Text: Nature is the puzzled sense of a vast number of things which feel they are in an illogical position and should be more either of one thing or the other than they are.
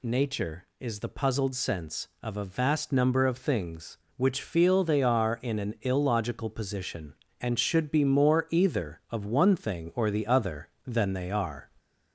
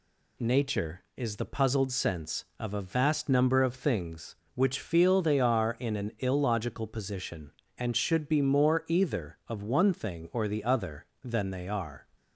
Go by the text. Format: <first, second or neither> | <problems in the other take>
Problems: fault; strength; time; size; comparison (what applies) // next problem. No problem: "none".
second | gets louder; slight; throughout; 2.5 dB